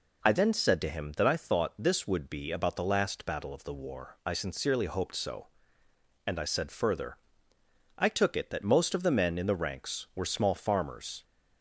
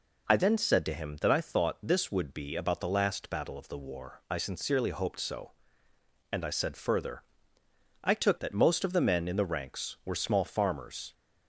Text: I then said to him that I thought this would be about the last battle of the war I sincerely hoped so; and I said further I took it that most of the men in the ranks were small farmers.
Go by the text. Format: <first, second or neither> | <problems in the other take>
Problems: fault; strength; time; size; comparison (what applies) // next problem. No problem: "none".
first | pauses between "further" and "I"; noticeable; at 7.2 s; 0.80 s long; noticeable in the first // skips "it"; at 8.3 s